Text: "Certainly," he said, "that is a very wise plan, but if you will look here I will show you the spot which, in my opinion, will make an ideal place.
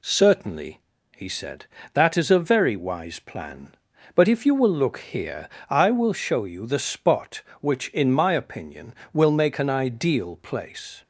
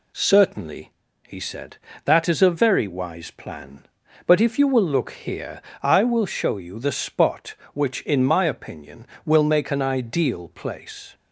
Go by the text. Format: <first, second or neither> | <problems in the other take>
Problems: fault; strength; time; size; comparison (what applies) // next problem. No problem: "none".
neither | pauses between "here" and "I"; slight; the same in both